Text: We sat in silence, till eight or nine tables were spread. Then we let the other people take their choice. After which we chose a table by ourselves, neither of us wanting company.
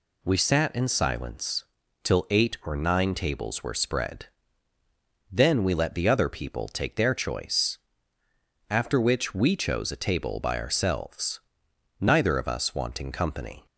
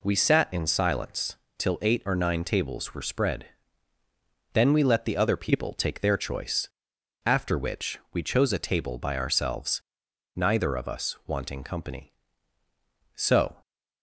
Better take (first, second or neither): first